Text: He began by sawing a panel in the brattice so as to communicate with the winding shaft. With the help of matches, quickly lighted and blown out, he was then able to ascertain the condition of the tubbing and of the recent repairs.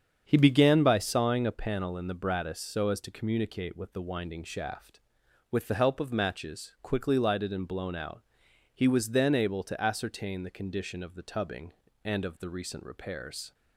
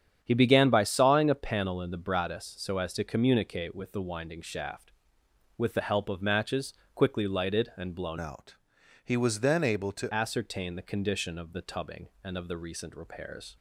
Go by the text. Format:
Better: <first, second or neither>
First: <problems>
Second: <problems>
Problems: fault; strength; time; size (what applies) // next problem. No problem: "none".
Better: first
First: starts louder than the rest; strong; until 1.2 s; 7.5 dB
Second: starts louder than the rest; strong; until 1.2 s; 8.5 dB // changes voice from "out" to "to"; from 8.2 to 10.1 s; 1.9 s long